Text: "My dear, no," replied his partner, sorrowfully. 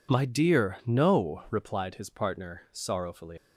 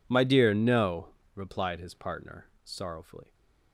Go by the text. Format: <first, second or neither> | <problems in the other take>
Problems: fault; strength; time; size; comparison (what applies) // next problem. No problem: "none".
second | leaves "sorrowfully" unfinished; at 3.3 s; 120 ms